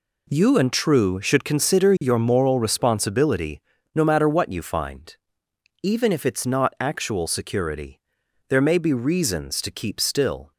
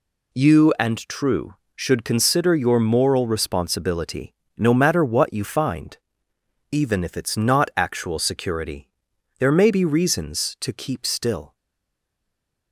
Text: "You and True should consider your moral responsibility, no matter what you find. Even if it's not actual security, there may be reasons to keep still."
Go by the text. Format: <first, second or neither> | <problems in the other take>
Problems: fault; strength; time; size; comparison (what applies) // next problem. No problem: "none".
first | stays silent after the last word; noticeable; from 11.5 s on; 1.2 s long